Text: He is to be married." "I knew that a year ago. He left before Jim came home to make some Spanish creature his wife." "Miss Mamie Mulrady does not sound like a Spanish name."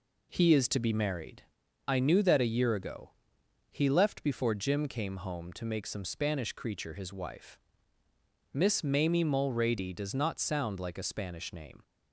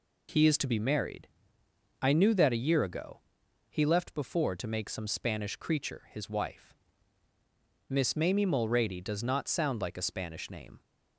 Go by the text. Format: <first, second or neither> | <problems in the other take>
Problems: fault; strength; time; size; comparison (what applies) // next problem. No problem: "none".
first | skips "Jim came home"; at 4.5 s